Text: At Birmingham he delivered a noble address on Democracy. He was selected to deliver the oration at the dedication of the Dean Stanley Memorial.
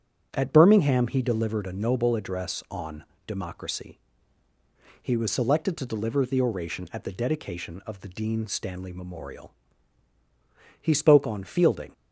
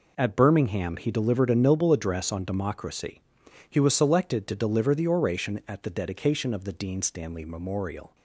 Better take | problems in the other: second | starts louder than the rest; strong; until 1.3 s; 7.5 dB // pauses between "on" and "Democracy"; slight; at 3.0 s; 0.24 s long // goes on to say "He spoke on Fielding"; noticeable; from 10.8 s on; 1.1 s long

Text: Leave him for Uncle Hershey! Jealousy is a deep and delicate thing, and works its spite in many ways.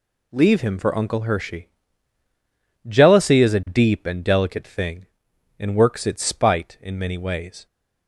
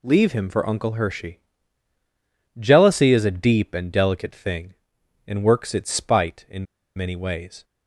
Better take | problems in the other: first | pauses between "in" and "many"; slight; at 6.6 s; 0.30 s long

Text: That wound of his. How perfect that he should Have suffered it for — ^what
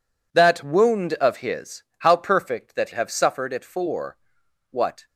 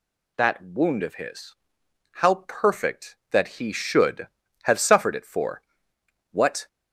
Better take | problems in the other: second | skips "he should"; at 2.9 s

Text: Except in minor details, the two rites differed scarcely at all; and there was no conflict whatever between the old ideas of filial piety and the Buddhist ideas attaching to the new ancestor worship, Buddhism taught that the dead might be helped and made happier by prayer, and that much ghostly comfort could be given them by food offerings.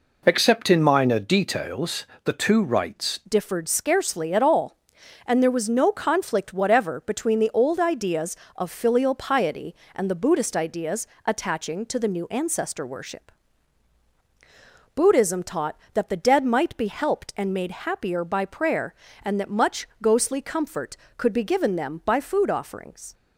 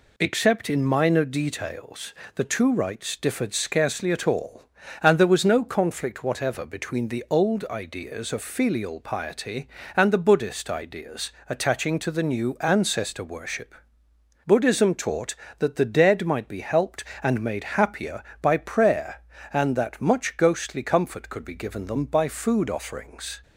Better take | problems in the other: second | changes voice at "differed"; from 3.2 s on; 19.9 s long // pauses between "ideas" and "attaching"; slight; at 11.0 s; 0.18 s long; slight in the second // pauses between "much" and "ghostly"; slight; at 19.8 s; 0.16 s long

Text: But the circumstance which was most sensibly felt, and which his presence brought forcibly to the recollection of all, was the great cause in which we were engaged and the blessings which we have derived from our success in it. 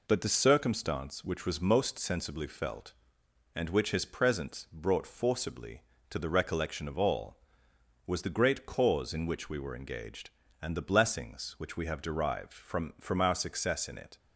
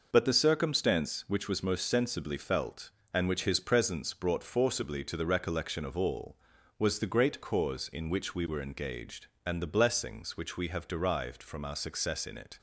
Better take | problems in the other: second | says "from" twice; at 13.0 s

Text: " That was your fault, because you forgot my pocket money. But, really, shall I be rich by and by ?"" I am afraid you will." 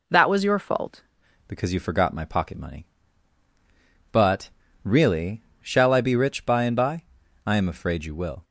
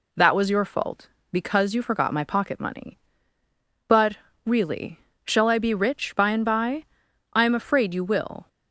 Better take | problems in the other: second | changes voice at "because"; from 1.4 s on; 7.0 s long

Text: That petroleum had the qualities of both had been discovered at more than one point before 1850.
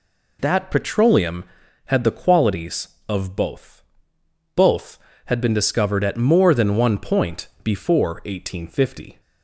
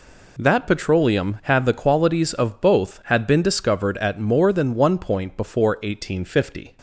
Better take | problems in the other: second | says "both" twice; at 4.5 s

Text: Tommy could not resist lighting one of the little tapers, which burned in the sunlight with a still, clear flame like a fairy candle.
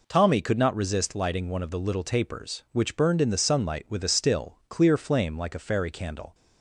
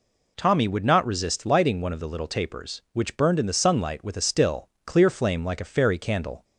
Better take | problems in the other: first | says "would" for "could"; at 0.6 s

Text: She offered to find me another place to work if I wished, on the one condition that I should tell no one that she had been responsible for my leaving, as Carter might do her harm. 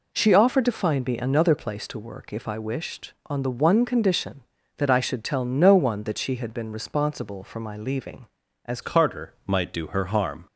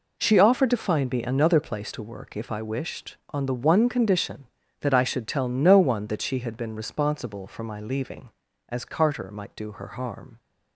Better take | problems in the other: second | changes voice at "Carter"; from 8.8 s on; 1.6 s long

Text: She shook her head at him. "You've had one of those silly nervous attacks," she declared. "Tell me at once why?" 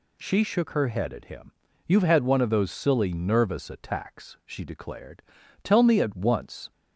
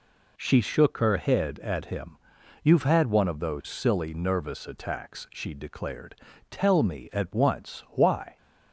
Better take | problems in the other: second | stops before "why"; at 6.7 s

